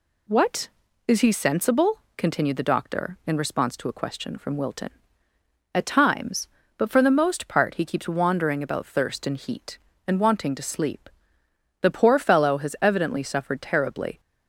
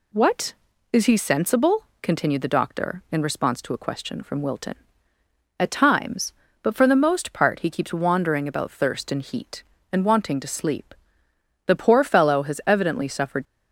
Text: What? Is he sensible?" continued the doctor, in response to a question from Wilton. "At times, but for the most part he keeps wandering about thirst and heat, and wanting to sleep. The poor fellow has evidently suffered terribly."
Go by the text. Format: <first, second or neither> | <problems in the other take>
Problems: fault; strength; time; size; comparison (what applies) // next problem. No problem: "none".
first | stops before "terribly"; at 13.4 s